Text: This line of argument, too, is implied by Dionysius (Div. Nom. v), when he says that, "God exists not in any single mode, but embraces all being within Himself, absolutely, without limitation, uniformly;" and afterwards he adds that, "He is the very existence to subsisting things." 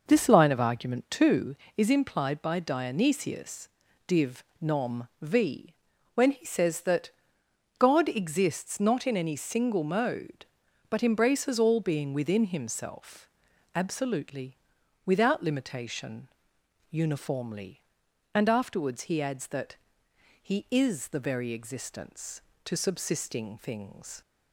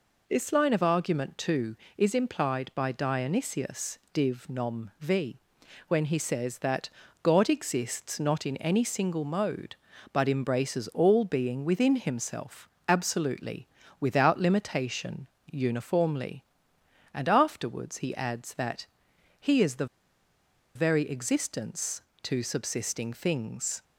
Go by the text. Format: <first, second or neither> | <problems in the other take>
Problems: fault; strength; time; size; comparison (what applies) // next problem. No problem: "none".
first | pauses between "the" and "very"; noticeable; at 19.8 s; 0.89 s long